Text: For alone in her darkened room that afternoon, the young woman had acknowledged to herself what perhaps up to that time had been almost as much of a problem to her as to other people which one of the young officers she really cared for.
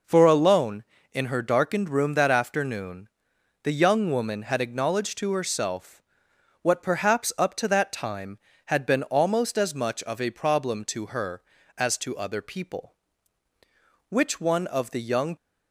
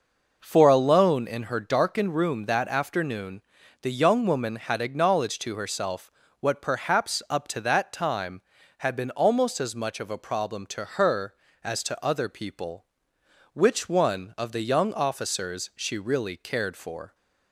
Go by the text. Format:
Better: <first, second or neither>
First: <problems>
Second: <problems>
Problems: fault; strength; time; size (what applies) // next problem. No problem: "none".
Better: second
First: pauses between "herself" and "what"; noticeable; at 6.0 s; 0.58 s long // stops before "officers she really cared for"; at 15.3 s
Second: pauses between "herself" and "what"; slight; at 6.1 s; 0.30 s long